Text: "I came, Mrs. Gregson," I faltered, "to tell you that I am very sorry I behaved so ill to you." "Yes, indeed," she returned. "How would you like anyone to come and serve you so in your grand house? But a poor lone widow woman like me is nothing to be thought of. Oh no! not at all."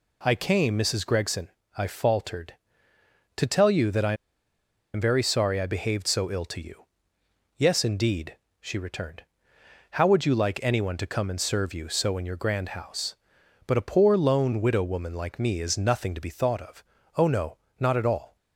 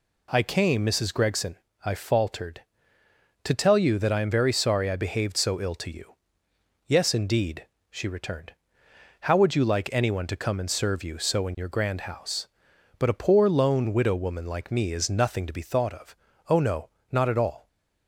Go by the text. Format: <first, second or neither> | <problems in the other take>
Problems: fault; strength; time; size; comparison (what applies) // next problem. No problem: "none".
second | pauses between "I" and "am"; noticeable; at 4.1 s; 0.80 s long